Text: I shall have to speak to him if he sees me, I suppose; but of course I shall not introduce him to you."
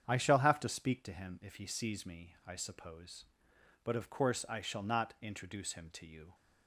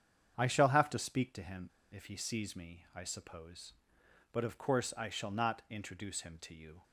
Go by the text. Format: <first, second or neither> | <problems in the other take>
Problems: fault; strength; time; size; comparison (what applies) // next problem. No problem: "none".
first | starts louder than the rest; strong; until 1.3 s; 8 dB; strong in the first // pauses between "him" and "if"; slight; at 1.6 s; 0.22 s long